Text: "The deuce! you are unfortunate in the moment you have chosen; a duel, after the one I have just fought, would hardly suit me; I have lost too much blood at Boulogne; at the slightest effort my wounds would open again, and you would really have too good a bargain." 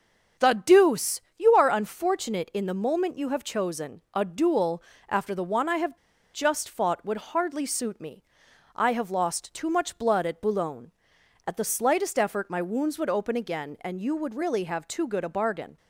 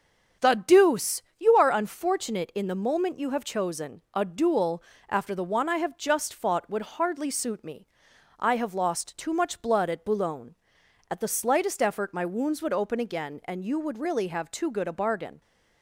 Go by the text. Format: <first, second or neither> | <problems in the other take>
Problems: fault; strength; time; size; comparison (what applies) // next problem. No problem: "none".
second | starts louder than the rest; strong; until 1.6 s; 7.5 dB; strong in the second // pauses between "have" and "just"; at 5.9 s; 0.36 s long